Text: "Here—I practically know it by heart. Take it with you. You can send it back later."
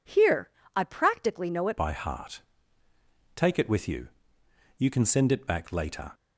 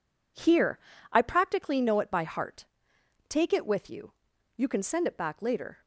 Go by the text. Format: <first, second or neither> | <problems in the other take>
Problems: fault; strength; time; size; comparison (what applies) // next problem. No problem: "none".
second | changes voice at "by"; from 1.7 s on; 4.4 s long